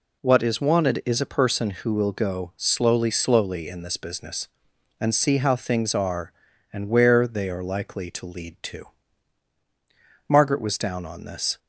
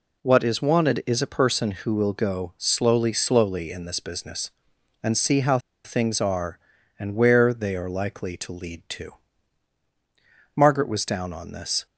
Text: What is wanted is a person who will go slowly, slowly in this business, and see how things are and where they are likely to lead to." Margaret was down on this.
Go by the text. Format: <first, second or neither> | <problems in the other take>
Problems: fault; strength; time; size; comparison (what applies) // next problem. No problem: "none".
first | pauses between "how" and "things"; slight; at 5.6 s; 0.24 s long